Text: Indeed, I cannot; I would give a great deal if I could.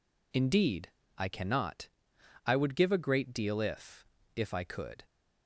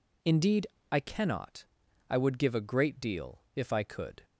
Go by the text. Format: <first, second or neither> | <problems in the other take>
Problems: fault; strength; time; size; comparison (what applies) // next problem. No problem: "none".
second | says "if" twice; at 4.3 s